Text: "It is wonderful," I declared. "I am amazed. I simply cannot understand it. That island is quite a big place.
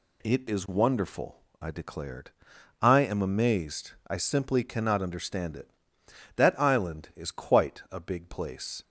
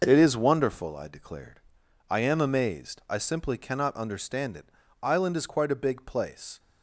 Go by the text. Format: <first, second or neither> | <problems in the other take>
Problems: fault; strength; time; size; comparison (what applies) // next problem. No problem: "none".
first | starts louder than the rest; noticeable; until 1.0 s; 6 dB // skips "That"; at 4.8 s